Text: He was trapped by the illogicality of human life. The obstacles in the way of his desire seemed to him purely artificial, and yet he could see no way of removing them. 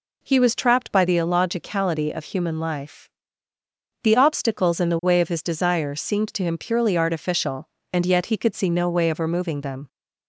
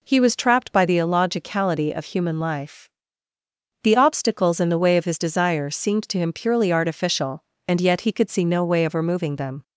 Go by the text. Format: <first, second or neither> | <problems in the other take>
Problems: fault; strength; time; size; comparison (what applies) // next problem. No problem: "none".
neither | none